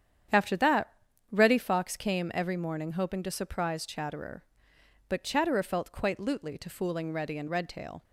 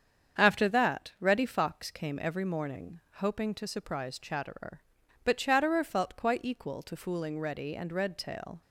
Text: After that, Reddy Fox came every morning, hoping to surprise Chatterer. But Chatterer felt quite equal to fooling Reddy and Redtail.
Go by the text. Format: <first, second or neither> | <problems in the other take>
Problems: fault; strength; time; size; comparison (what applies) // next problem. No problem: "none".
second | starts louder than the rest; strong; until 1.7 s; 9 dB; strong in the second // says "lutely" for "equal"; at 6.1 s